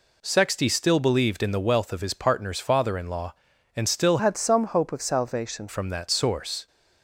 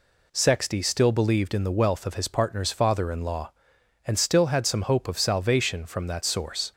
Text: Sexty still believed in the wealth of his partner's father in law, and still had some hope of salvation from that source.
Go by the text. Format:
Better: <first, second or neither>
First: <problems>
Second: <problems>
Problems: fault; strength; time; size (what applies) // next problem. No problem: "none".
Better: second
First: changes voice from "had" to "salvation"; from 4.1 to 5.6 s; 1.5 s long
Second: none